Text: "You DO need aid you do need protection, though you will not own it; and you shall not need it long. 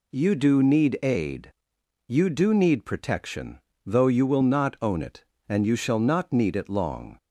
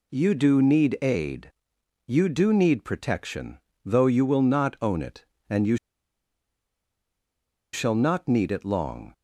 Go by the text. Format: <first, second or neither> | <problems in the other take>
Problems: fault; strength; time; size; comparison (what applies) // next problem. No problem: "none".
first | pauses between "aid" and "you"; noticeable; at 1.5 s; 0.54 s long; noticeable in the first // pauses between "you" and "shall"; strong; at 5.7 s; 1.9 s long